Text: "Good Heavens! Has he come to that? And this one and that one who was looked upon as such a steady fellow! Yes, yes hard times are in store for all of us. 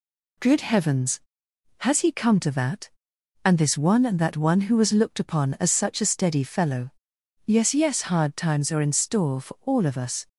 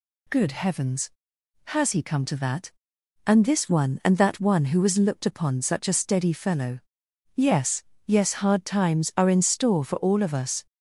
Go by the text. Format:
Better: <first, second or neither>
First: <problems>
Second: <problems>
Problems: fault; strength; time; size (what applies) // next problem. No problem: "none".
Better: first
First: none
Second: skips "as"; at 5.6 s